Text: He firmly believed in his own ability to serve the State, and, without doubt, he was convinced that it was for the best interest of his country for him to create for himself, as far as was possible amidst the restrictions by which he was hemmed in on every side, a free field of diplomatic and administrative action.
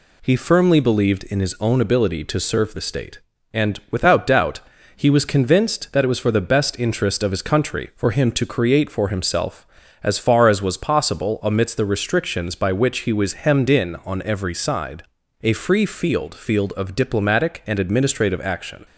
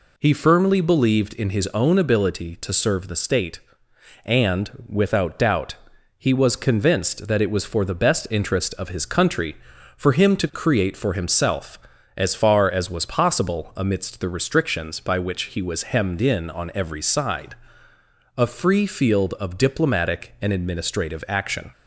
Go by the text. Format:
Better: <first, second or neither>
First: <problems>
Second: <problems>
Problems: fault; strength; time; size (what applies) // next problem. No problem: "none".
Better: second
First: says "field" twice; at 16.3 s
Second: none